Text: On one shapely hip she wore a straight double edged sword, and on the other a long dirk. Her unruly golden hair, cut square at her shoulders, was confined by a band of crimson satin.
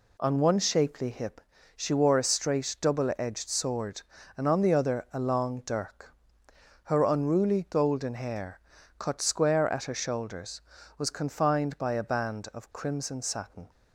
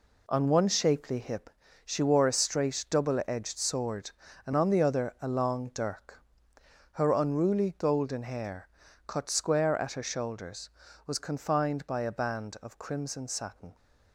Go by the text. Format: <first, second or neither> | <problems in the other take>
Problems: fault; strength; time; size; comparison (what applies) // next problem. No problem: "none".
first | gets quieter; strong; throughout; 8.5 dB // pauses between "hip" and "she"; slight; at 1.5 s; 0.34 s long; slight in the first